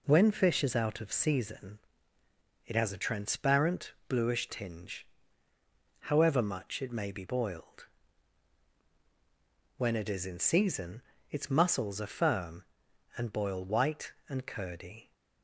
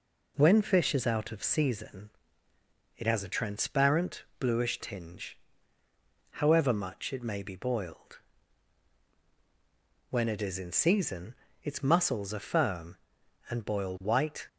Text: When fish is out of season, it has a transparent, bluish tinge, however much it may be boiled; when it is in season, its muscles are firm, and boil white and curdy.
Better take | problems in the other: first | stops before "and curdy"; at 14.4 s

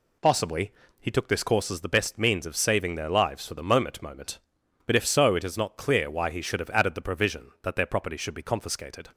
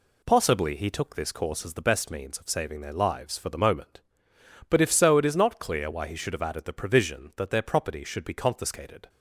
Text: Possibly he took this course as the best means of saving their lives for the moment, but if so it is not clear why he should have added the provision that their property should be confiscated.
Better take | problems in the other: second | pauses between "Possibly" and "he"; slight; at 0.7 s; 0.28 s long // says "moment" twice; at 4.0 s

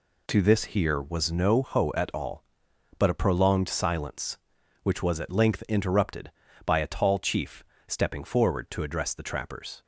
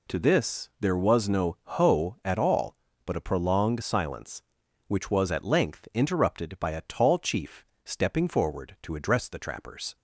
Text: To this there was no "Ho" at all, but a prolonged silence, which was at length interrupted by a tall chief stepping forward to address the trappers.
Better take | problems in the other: second | says "here" for "there"; at 0.6 s // pauses between "chief" and "stepping"; slight; at 7.6 s; 0.24 s long; slight in the second

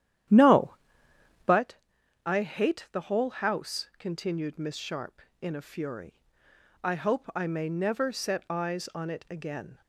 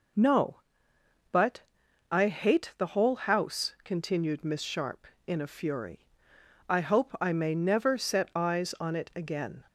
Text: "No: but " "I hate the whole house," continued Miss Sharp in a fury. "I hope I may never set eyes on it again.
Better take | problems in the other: second | starts louder than the rest; strong; until 1.6 s; 11 dB

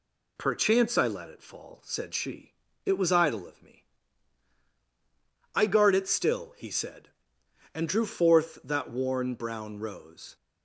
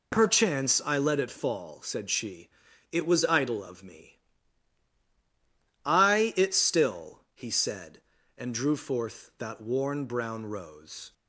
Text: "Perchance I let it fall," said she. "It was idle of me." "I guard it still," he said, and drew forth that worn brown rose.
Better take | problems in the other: first | skips "guard"; at 6.3 s

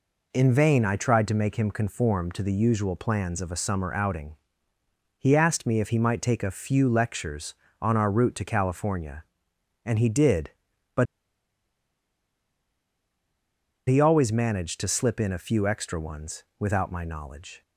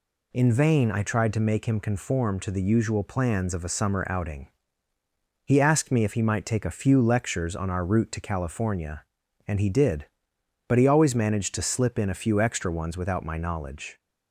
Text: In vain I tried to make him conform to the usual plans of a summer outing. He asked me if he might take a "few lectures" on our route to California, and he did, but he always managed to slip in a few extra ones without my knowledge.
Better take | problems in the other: second | pauses between "but" and "he"; strong; at 11.0 s; 2.8 s long

